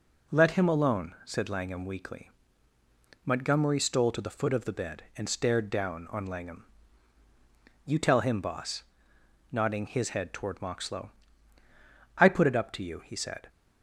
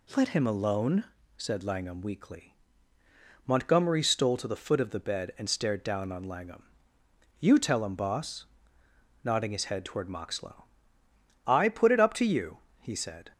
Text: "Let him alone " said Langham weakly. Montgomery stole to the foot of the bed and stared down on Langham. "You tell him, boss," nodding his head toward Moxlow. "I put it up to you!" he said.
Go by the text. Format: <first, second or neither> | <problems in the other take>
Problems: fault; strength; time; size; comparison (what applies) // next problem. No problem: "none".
neither | none